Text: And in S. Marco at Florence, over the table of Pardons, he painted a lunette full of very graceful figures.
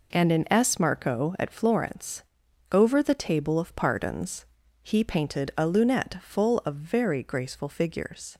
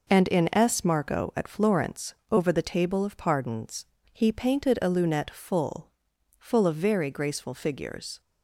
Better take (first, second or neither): first